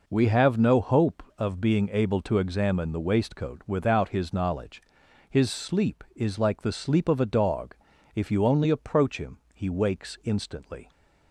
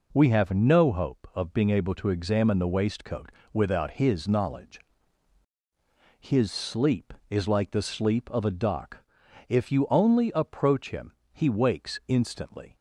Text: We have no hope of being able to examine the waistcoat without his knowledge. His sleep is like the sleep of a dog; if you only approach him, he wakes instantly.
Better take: first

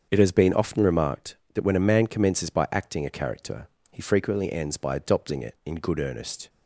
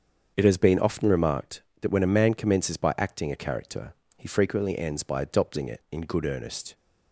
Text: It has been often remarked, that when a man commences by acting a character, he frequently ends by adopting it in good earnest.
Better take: neither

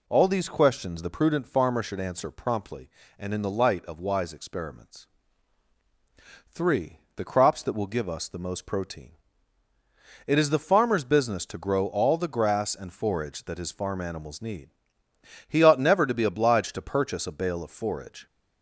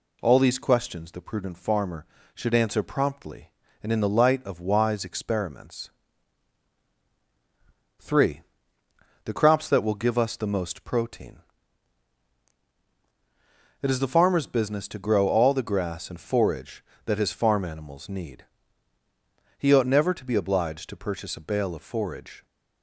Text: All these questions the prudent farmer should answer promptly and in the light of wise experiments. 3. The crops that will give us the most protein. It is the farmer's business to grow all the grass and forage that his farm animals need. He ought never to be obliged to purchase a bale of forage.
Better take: neither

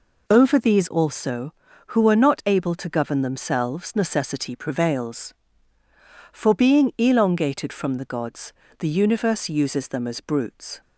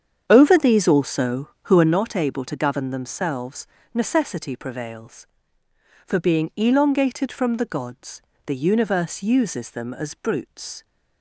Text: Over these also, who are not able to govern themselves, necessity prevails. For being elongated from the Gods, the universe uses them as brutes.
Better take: first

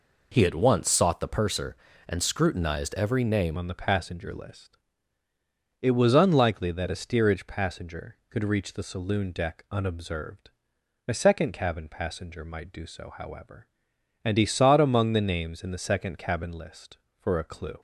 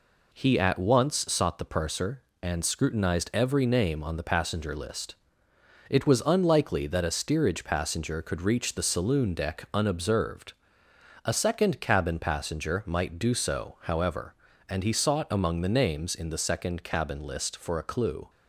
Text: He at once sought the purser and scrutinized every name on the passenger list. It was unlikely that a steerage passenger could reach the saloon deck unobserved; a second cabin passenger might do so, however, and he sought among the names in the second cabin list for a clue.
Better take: second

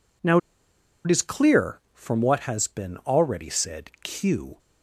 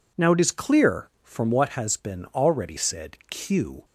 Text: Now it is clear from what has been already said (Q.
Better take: second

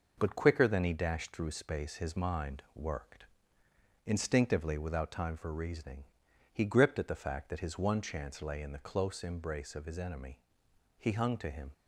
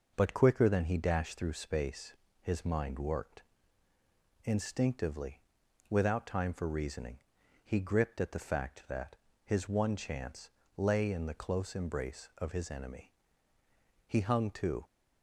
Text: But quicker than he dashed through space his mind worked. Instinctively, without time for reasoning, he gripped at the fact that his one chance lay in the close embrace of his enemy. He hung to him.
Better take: first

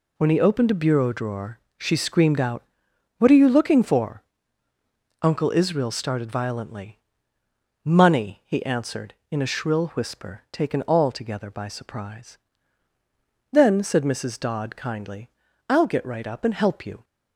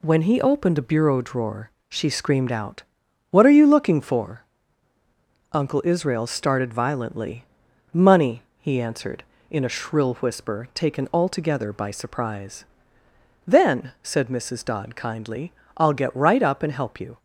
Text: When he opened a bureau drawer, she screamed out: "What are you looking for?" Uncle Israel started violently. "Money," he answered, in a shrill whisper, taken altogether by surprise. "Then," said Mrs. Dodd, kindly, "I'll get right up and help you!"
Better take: neither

